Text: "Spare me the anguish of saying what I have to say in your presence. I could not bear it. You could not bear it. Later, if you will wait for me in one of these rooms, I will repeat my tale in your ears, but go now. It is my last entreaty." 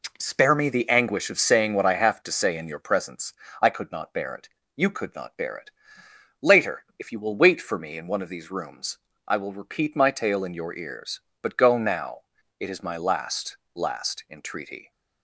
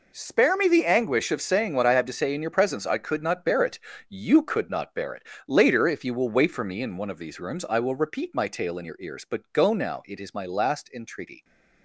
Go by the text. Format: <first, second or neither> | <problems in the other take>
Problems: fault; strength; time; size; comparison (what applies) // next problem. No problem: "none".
second | says "last" twice; at 13.7 s